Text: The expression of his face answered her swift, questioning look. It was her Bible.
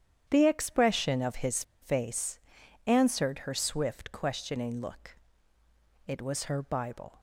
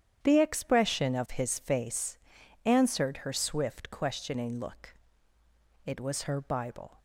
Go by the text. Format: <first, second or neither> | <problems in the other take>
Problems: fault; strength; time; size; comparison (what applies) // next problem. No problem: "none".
second | starts louder than the rest; strong; until 1.3 s; 9.5 dB; strong in the second // pauses between "his" and "face"; slight; at 1.6 s; 0.18 s long // pauses between "face" and "answered"; noticeable; at 2.3 s; 0.48 s long; noticeable in the second